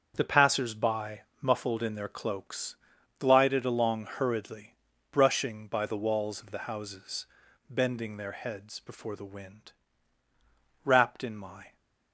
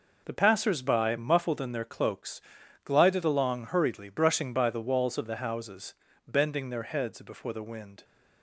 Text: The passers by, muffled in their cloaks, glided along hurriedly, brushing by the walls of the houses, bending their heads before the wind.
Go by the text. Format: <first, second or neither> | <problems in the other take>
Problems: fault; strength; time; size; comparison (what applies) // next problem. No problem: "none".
second | starts louder than the rest; until 1.1 s; 7 dB // goes on to say "Wrapped in my"; noticeable; from 10.8 s on; 0.90 s long